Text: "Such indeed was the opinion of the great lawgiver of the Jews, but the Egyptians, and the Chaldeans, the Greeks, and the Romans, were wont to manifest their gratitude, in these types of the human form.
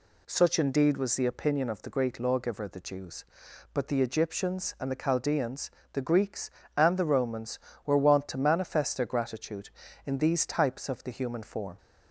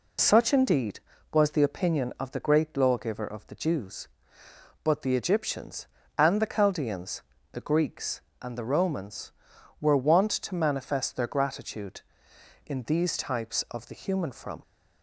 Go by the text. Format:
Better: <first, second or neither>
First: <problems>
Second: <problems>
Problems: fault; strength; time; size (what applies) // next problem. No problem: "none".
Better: first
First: none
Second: says "from" for "form"; at 14.3 s